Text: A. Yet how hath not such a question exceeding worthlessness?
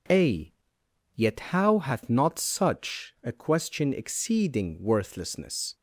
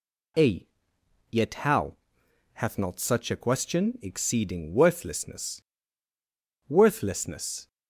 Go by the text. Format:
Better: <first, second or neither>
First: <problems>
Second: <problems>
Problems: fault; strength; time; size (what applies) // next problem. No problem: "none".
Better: first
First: none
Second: pauses between "how" and "hath"; noticeable; at 1.9 s; 0.56 s long // says "worthlessness" twice; at 6.6 s